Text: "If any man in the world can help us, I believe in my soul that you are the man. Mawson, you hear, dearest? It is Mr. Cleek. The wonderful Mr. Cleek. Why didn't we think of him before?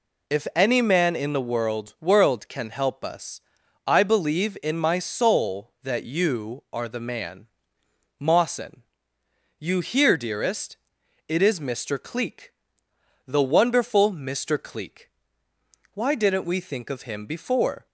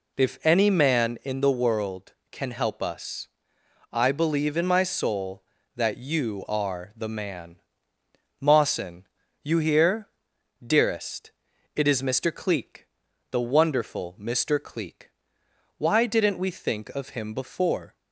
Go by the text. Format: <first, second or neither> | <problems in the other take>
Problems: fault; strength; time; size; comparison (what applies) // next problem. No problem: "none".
second | says "world" twice; at 1.9 s